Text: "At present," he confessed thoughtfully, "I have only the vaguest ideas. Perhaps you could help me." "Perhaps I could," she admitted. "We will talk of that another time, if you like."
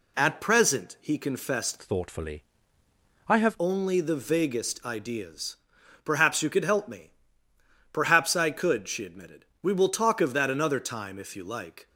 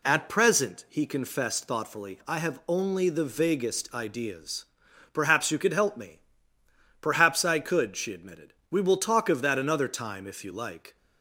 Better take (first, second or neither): second